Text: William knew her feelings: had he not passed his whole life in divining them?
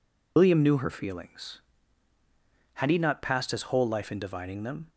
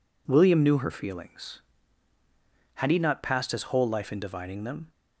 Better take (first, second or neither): second